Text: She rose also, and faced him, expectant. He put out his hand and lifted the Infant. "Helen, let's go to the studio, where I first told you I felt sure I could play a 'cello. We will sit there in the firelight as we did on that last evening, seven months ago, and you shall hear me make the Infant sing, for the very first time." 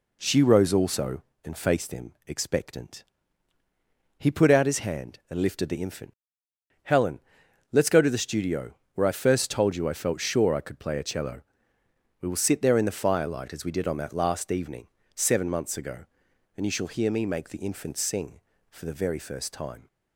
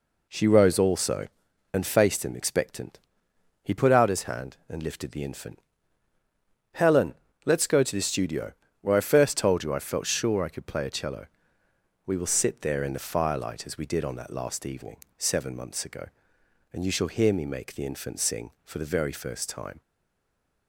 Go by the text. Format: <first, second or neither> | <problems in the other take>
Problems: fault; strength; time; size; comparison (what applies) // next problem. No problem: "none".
first | stays silent after the last word; slight; from 19.8 s on; 0.8 s long